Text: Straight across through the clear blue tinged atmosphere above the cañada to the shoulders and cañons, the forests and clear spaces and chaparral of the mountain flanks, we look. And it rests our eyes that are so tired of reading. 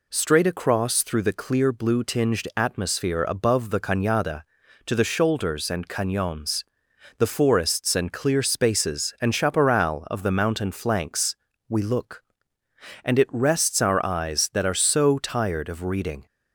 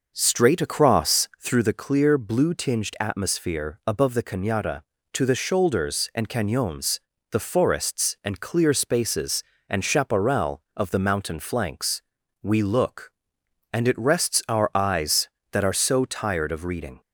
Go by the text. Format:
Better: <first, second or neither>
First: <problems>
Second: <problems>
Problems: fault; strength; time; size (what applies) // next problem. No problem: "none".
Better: first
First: none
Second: starts louder than the rest; noticeable; until 1.7 s; 6 dB